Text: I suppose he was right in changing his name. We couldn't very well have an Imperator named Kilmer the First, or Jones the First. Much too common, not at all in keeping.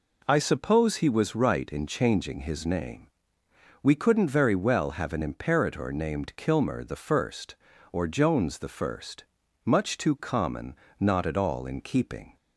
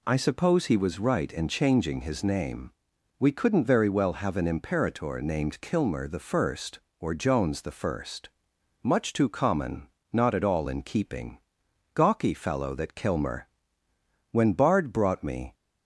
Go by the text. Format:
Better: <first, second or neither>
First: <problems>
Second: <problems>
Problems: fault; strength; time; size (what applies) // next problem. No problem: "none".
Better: first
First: none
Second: goes on to say "Gawky fellow that Kilmer When Bard brought me"; strong; from 11.9 s on; 3.6 s long